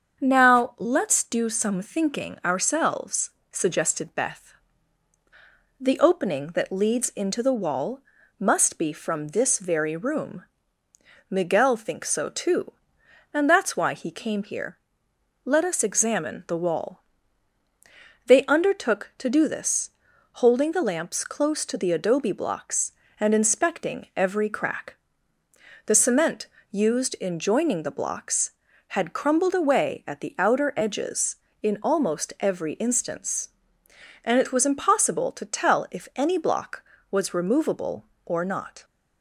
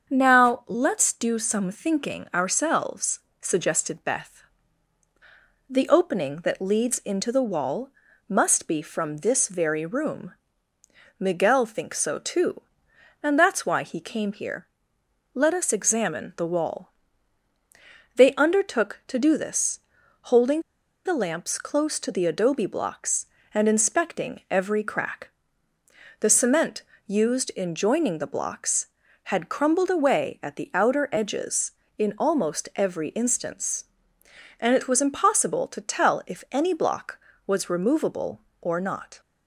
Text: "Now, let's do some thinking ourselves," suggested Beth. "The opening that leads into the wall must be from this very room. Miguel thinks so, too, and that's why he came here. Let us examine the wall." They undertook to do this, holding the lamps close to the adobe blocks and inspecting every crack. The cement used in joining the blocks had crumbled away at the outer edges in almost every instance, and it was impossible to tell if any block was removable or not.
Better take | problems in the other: first | starts louder than the rest; until 1.1 s; 7 dB; also in the first // pauses between "wall" and "must"; at 7.8 s; 0.38 s long; also in the first // pauses between "holding" and "the"; at 20.6 s; 0.43 s long // pauses between "cement" and "used"; slight; at 26.8 s; 0.24 s long; slight in the first

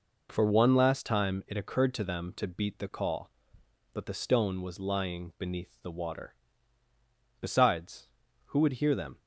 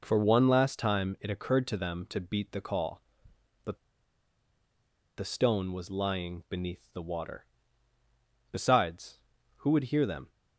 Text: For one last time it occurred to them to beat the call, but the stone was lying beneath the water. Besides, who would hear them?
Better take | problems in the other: first | pauses between "but" and "the"; strong; at 3.7 s; 1.4 s long

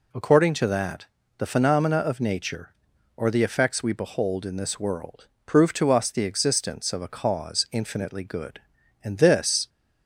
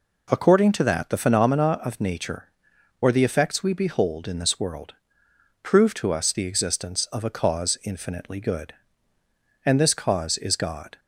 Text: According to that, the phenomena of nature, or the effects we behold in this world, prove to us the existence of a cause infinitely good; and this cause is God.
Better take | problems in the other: second | stops before "cause is God"; at 9.6 s

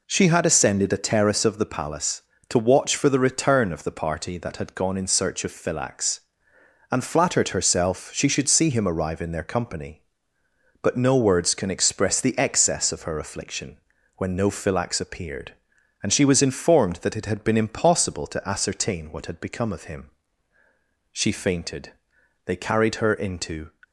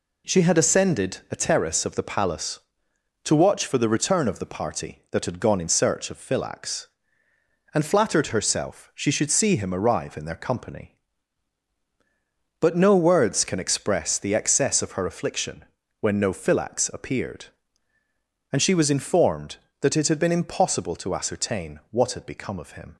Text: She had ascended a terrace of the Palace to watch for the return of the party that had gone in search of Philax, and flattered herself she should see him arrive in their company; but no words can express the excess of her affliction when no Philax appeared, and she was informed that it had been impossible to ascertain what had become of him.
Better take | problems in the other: second | pauses between "affliction" and "when"; at 13.7 s; 0.38 s long; slight in the second // goes on to say "She fainted they carried her into"; strong; from 21.1 s on; 2.5 s long

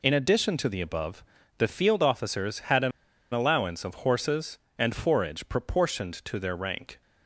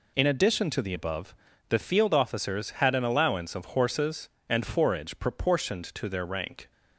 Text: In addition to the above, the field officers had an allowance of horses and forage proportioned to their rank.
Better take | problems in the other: second | pauses between "an" and "allowance"; at 2.9 s; 0.41 s long

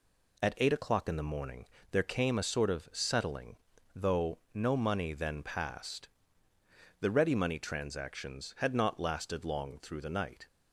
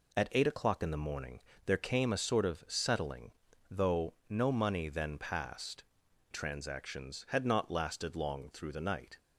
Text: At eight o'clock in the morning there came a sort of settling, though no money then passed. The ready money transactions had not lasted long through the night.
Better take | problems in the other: first | pauses between "morning" and "there"; slight; at 1.3 s; 0.24 s long; slight in the first // pauses between "though" and "no"; slight; at 4.1 s; 0.16 s long; slight in the first // skips "The ready money"; at 6.0 s

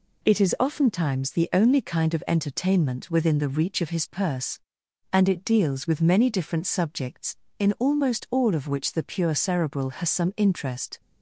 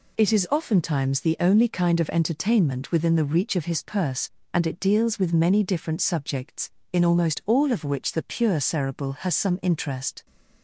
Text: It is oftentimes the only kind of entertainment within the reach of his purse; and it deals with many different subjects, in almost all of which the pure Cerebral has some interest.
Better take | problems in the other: neither | none

